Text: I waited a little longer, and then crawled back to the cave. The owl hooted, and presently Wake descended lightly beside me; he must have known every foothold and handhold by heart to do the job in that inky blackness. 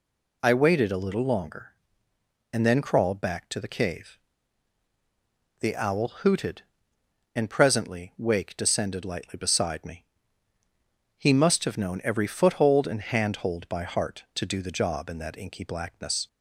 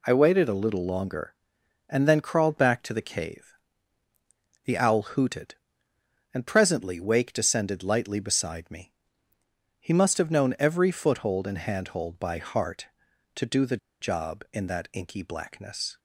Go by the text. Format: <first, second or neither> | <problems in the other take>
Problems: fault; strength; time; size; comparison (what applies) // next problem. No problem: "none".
first | pauses between "the" and "job"; slight; at 13.7 s; 0.24 s long